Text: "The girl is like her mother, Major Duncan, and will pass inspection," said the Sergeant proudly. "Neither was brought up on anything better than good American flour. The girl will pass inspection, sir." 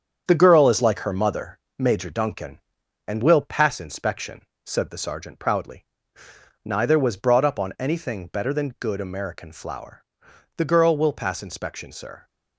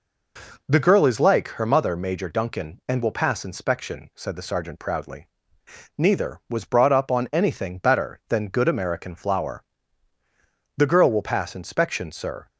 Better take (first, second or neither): second